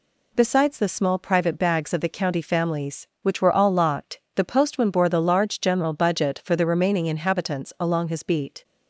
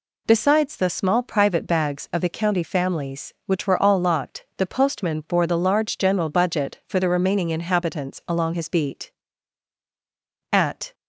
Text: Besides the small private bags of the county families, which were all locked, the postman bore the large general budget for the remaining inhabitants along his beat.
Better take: first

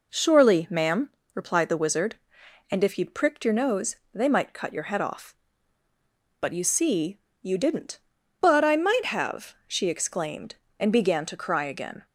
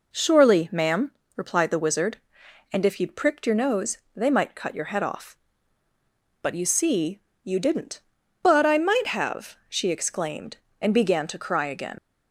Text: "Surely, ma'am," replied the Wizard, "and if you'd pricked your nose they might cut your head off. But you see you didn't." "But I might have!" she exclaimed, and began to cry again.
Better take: first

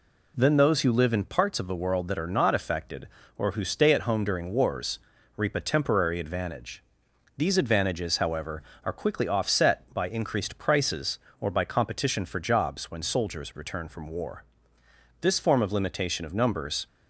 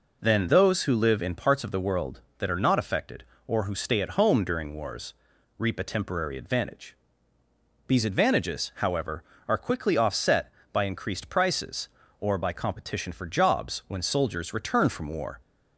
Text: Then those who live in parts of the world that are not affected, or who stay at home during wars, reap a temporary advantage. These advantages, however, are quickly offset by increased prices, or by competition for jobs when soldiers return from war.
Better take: second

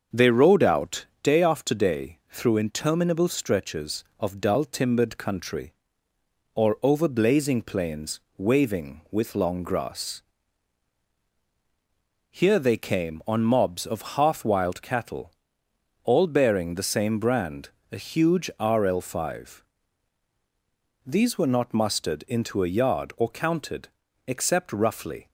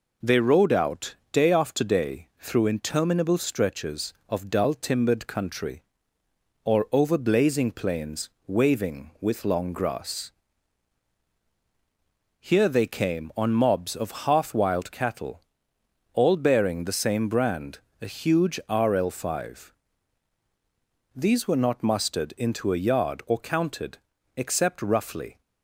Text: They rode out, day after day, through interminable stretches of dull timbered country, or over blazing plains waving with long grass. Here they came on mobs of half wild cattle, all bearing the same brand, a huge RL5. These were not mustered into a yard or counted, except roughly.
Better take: second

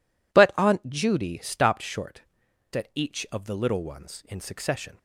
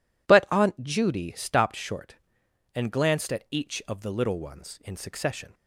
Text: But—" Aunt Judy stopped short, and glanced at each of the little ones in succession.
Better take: second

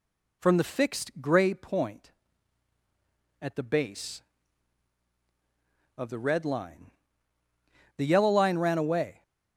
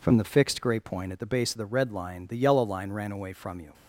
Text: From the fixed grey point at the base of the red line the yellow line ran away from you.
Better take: second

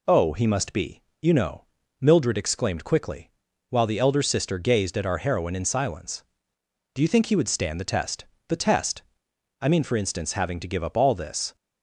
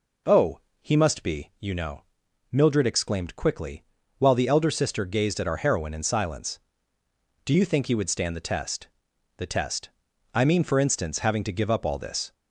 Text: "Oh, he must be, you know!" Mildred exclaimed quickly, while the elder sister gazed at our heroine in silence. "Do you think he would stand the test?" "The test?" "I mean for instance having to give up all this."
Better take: neither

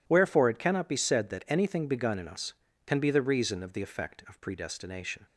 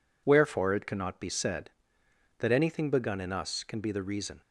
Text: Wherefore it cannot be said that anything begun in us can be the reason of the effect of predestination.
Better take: first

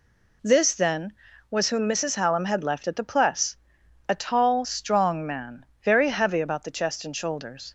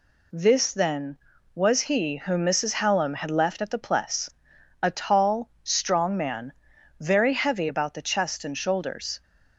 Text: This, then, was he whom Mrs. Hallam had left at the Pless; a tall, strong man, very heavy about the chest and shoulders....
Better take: second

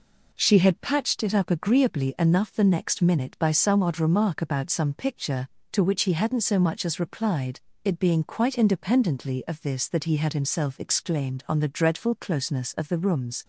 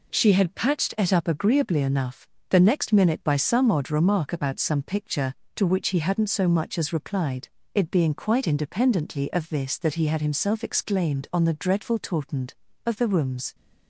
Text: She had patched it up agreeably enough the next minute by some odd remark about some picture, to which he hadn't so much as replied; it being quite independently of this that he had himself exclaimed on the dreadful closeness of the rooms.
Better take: first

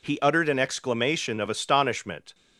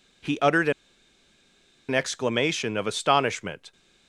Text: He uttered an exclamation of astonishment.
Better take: first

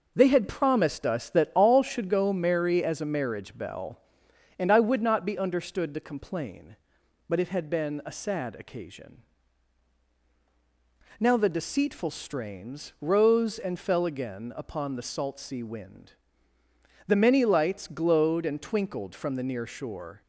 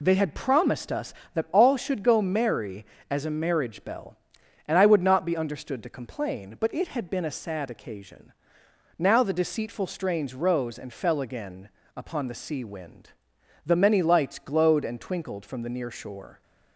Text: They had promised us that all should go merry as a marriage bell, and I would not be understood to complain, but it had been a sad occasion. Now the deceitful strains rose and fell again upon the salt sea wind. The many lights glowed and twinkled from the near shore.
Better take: first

